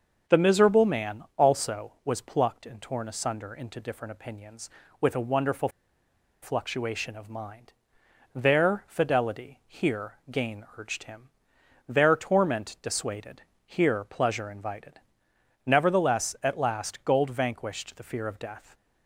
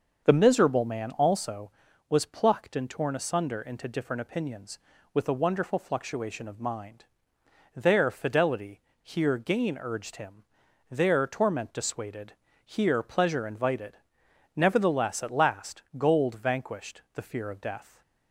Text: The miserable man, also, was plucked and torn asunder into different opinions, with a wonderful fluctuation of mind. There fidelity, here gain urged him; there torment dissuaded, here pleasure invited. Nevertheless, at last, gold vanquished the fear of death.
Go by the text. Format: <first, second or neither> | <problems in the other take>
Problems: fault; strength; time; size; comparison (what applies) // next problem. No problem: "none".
second | starts louder than the rest; until 1.4 s; 7 dB; also in the second // pauses between "wonderful" and "fluctuation"; noticeable; at 5.6 s; 0.73 s long // pauses between "here" and "gain"; slight; at 10.1 s; 0.16 s long